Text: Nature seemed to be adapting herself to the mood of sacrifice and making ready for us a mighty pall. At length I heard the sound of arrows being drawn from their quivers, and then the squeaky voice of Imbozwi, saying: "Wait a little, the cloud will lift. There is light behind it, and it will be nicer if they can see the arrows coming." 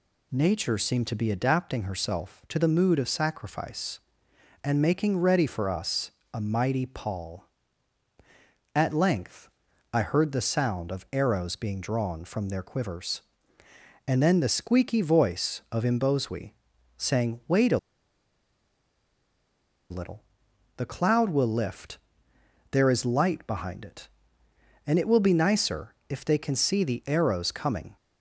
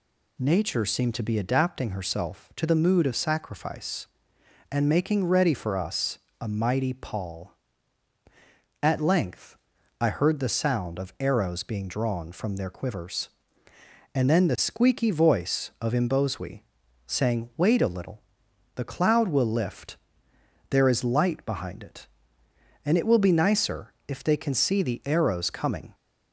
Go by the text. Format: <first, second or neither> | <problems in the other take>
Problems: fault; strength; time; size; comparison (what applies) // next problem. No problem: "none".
second | pauses between "us" and "a"; slight; at 6.1 s; 0.22 s long; slight in the second // pauses between "length" and "I"; at 9.4 s; 0.44 s long; also in the second // pauses between "a" and "little"; strong; at 17.7 s; 2.1 s long // pauses between "nicer" and "if"; slight; at 25.9 s; 0.16 s long; slight in the second